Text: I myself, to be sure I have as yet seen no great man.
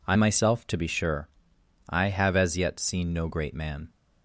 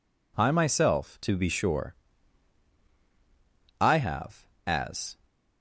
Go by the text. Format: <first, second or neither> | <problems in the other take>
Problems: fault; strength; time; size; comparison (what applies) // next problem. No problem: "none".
first | pauses between "sure" and "I"; strong; at 1.9 s; 1.8 s long; noticeable in the first // stops before "yet seen no great man"; at 5.2 s